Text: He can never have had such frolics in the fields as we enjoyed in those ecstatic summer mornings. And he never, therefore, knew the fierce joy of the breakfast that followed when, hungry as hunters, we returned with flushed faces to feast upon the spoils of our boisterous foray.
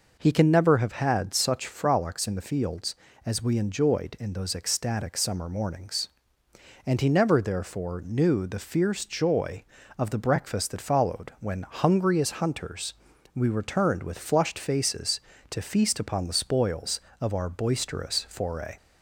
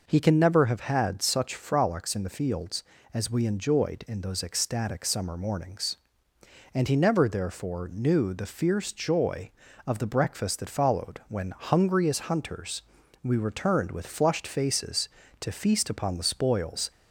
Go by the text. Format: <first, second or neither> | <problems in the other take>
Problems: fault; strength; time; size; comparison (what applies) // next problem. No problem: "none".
first | stops before "of our boisterous foray"; at 16.9 s